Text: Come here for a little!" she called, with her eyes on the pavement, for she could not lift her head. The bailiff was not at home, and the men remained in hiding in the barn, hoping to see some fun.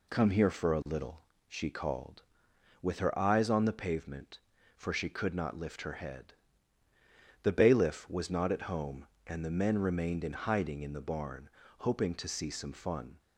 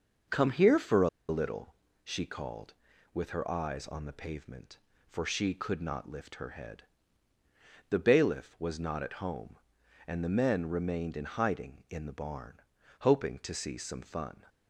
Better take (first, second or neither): first